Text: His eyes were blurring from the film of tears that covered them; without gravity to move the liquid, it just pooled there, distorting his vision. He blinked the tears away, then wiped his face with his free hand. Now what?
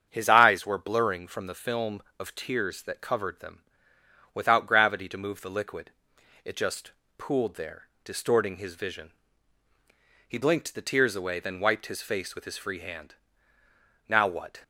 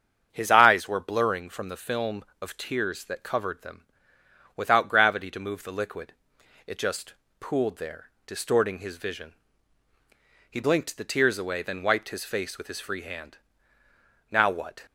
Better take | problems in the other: neither | starts louder than the rest; strong; the same in both // pauses between "just" and "pooled"; slight; the same in both

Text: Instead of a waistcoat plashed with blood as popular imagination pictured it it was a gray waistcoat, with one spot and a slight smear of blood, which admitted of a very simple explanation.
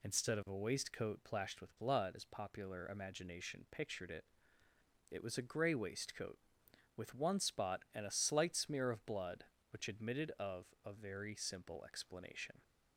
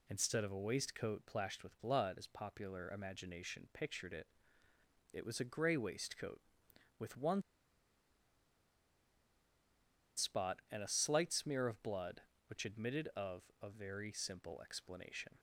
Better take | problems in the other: first | pauses between "it" and "it"; noticeable; at 4.2 s; 0.86 s long; noticeable in the first // pauses between "one" and "spot"; strong; at 7.4 s; 2.7 s long // pauses between "of" and "a"; slight; at 13.4 s; 0.22 s long; slight in the first

